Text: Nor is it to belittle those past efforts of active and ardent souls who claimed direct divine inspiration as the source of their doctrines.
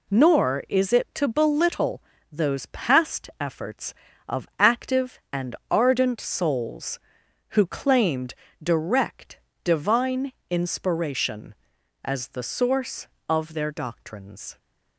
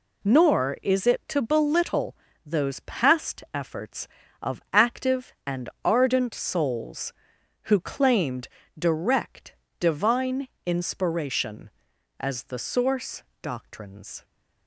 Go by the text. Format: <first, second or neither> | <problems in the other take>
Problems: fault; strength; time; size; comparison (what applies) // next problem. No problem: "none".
first | pauses between "belittle" and "those"; slight; at 2.1 s; 0.30 s long; slight in the first // pauses between "claimed" and "direct"; slight; at 8.4 s; 0.30 s long; slight in the first // pauses between "direct" and "divine"; slight; at 9.5 s; 0.26 s long; slight in the first // pauses between "divine" and "inspiration"; slight; at 10.4 s; 0.18 s long; slight in the first // skips "of their"; at 13.3 s